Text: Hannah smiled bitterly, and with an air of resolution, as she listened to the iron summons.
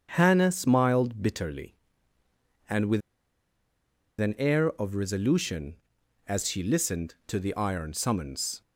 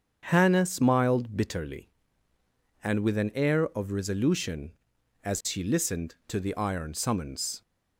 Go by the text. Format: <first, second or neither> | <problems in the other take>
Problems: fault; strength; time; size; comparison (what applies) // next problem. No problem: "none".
second | starts louder than the rest; strong; until 1.1 s; 7.5 dB; strong in the second // pauses between "with" and "an"; at 3.0 s; 1.2 s long